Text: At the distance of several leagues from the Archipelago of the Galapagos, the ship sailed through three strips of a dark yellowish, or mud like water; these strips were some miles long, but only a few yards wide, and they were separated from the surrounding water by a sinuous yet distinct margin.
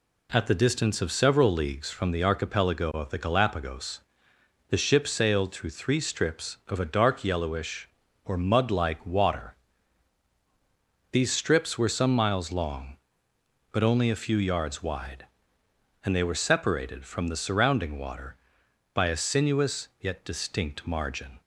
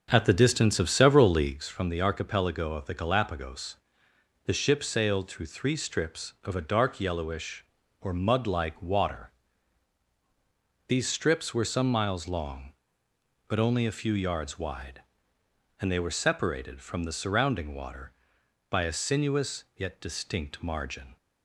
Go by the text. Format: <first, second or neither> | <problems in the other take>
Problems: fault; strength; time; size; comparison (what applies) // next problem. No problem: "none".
first | starts louder than the rest; until 1.6 s; 6.5 dB